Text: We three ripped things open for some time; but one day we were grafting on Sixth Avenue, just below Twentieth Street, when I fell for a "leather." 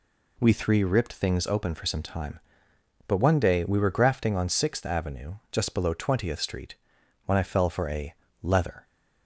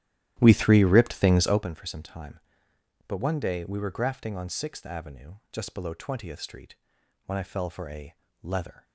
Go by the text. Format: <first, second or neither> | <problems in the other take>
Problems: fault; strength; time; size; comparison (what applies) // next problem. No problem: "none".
first | starts louder than the rest; strong; until 1.7 s; 13 dB // pauses between "a" and "leather"; slight; at 8.1 s; 0.28 s long; slight in the first